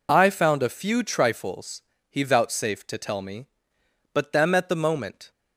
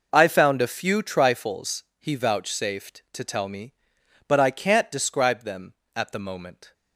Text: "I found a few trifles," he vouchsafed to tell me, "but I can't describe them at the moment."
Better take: second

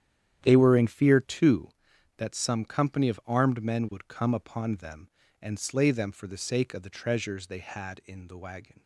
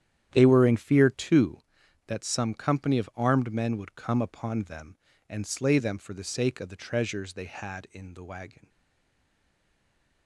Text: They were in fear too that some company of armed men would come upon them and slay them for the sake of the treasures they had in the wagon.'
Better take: first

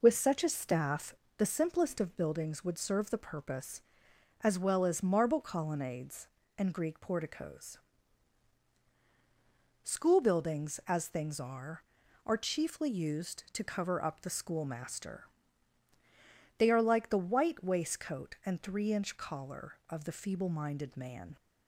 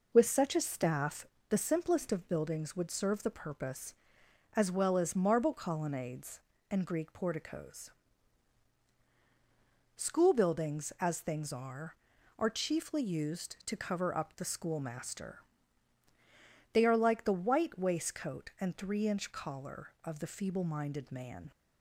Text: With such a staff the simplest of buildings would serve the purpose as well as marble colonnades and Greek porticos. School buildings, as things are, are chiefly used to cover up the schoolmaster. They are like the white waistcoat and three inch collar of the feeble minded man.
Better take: neither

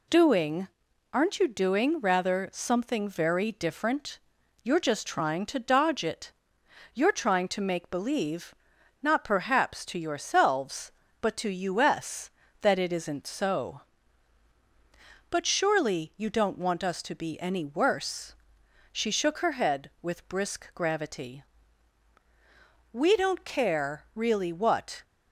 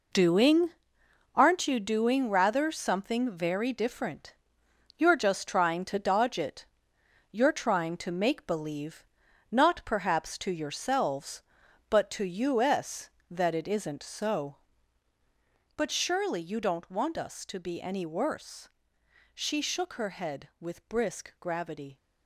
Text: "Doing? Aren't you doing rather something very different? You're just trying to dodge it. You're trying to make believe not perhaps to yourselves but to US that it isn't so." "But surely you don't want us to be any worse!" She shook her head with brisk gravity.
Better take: second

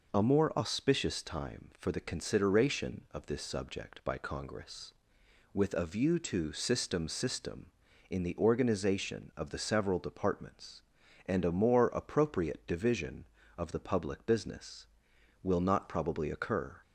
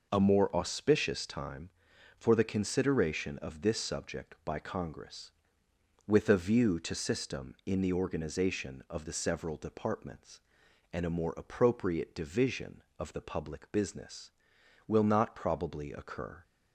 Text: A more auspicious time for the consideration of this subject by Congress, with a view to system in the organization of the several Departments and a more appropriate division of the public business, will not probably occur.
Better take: second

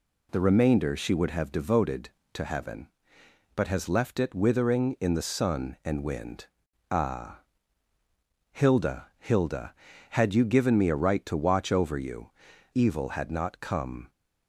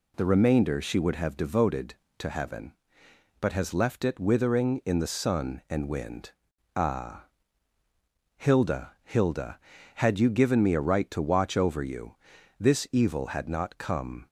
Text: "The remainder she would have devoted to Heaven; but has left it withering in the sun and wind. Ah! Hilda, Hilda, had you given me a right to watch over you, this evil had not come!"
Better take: second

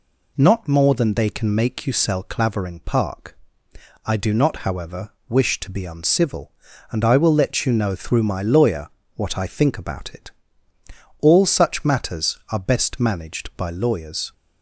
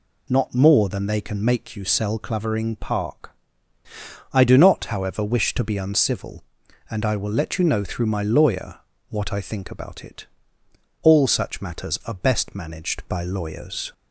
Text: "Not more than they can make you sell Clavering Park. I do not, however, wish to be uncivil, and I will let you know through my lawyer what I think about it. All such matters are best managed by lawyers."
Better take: neither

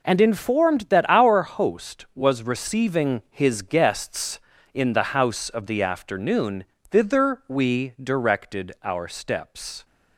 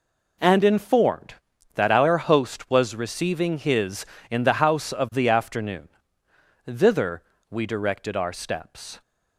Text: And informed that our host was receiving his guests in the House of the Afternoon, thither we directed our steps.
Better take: first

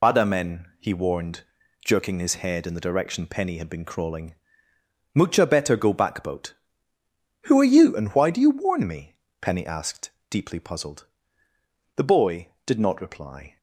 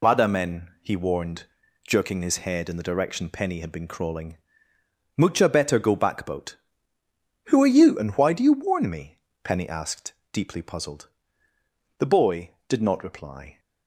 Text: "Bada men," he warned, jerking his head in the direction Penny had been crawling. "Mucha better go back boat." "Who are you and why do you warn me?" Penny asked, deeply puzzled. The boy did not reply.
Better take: second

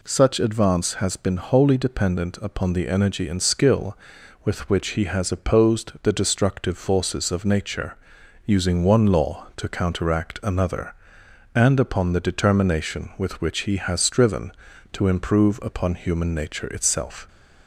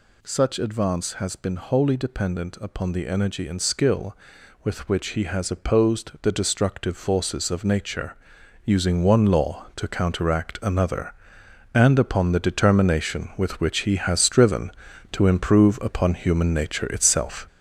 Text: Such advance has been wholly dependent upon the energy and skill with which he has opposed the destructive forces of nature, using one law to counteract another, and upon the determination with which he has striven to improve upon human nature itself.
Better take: first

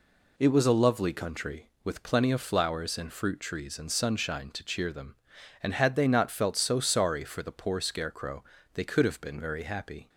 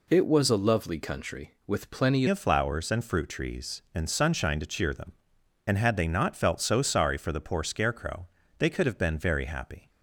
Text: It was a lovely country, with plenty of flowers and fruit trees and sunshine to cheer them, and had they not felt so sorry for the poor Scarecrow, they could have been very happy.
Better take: first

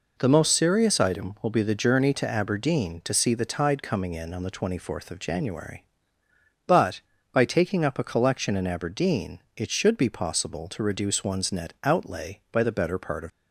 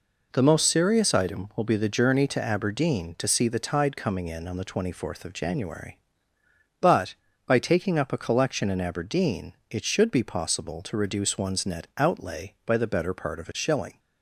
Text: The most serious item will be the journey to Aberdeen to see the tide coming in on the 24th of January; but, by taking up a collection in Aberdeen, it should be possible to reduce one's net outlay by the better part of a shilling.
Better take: second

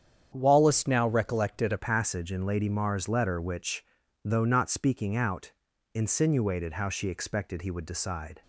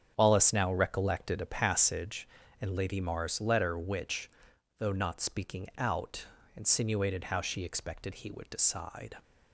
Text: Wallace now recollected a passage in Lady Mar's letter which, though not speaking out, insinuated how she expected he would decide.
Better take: second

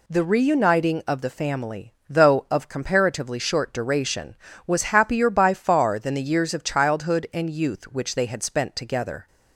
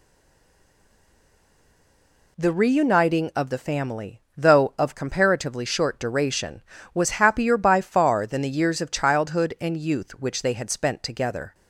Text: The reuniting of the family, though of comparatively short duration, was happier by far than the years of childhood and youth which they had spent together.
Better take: first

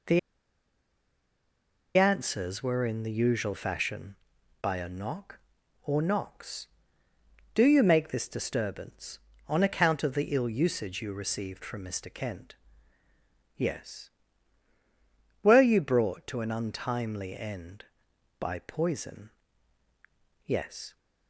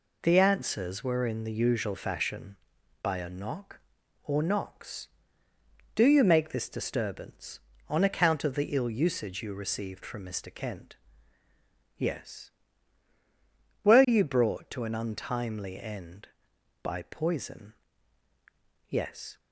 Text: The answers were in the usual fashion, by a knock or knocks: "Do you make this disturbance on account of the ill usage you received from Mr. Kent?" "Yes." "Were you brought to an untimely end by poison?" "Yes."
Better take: second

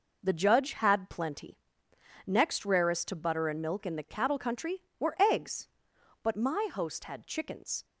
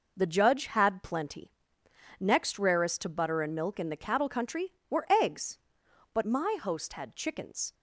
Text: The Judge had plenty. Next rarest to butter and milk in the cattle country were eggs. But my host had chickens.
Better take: neither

